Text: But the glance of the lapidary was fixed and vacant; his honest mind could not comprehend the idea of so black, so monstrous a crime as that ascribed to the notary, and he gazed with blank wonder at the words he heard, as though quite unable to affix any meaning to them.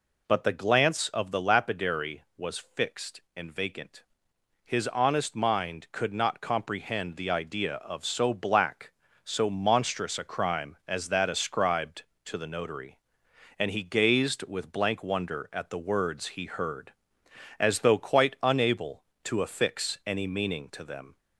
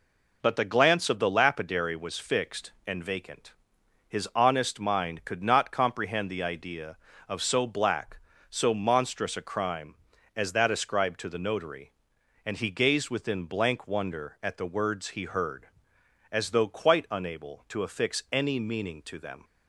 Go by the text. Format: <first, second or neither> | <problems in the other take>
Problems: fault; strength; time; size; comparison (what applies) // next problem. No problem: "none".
first | says "within" for "with"; at 13.0 s